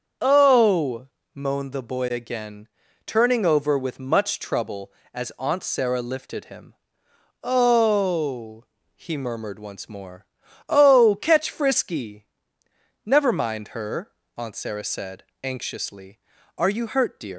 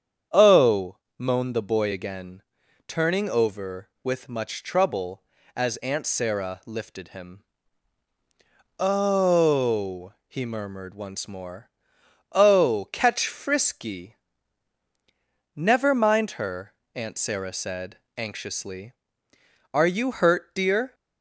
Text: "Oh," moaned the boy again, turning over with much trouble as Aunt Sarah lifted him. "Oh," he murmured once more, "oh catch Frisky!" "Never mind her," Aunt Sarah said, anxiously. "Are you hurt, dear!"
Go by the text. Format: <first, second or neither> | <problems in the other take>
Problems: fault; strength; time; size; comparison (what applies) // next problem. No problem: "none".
second | starts louder than the rest; until 1.4 s; 7 dB; strong in the second // leaves "dear" unfinished; at 17.3 s; 120 ms